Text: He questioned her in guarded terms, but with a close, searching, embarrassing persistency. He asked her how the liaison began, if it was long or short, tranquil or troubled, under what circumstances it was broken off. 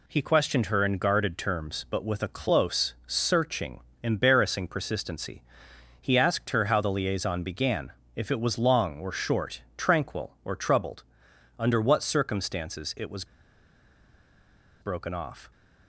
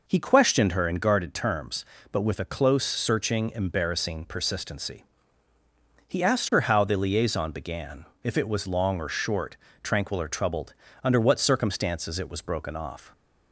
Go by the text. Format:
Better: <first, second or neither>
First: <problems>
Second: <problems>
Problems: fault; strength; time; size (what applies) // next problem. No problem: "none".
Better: second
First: pauses between "was" and "broken"; strong; at 13.2 s; 1.5 s long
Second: none